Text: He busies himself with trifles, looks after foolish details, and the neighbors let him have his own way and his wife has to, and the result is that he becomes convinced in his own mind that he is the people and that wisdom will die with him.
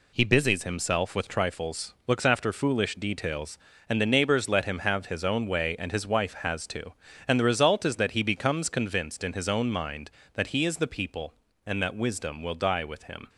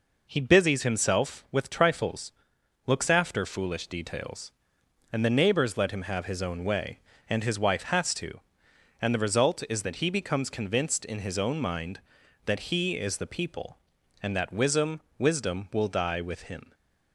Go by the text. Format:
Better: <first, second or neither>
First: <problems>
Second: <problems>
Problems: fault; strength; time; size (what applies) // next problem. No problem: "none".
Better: first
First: none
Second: says "wisdom" twice; at 15.1 s // stays silent after the last word; slight; from 16.6 s on; 0.5 s long